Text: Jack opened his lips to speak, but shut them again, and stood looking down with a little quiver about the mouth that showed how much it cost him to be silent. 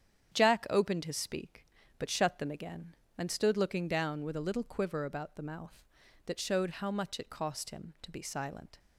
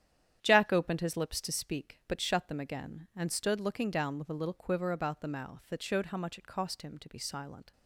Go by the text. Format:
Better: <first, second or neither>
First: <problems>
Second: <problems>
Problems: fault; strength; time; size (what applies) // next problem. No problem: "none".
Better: second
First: starts louder than the rest; strong; until 1.3 s; 8.5 dB // skips "lips to"; at 1.1 s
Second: starts louder than the rest; strong; until 1.4 s; 10 dB